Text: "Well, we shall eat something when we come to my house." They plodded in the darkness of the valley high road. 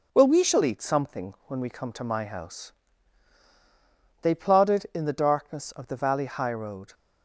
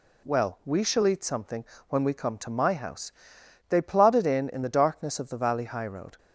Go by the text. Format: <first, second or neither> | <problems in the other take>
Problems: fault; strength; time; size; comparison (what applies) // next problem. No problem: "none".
first | pauses between "something" and "when"; slight; at 1.6 s; 0.24 s long // says "in" twice; at 4.5 s